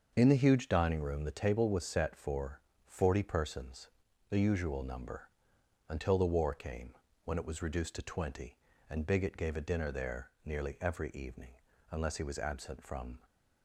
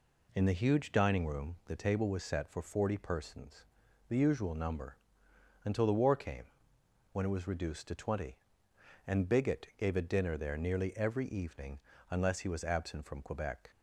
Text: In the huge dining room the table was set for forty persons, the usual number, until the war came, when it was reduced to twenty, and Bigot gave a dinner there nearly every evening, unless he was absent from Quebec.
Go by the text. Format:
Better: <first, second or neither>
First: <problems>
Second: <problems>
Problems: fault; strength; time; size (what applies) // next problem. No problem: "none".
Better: second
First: starts louder than the rest; until 1.1 s; 6.5 dB // pauses between "for" and "forty"; slight; at 2.6 s; 0.26 s long // pauses between "there" and "nearly"; slight; at 10.2 s; 0.16 s long // stops before "Quebec"; at 13.2 s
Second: none